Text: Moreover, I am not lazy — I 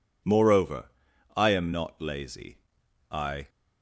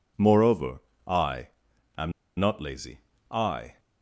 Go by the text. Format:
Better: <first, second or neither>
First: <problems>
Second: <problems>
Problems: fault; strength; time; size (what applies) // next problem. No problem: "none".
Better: first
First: none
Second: pauses between "I" and "am"; noticeable; at 1.4 s; 0.50 s long // pauses between "am" and "not"; slight; at 2.1 s; 0.27 s long